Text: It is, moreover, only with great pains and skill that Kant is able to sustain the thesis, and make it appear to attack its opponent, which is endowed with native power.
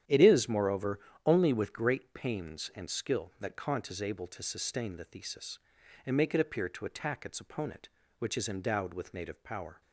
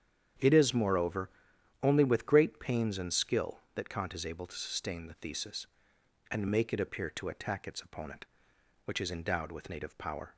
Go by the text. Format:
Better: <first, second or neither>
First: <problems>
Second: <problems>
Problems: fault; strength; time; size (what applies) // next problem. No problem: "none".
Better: neither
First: starts louder than the rest; strong; until 1.3 s; 10 dB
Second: starts louder than the rest; strong; until 1.9 s; 8.5 dB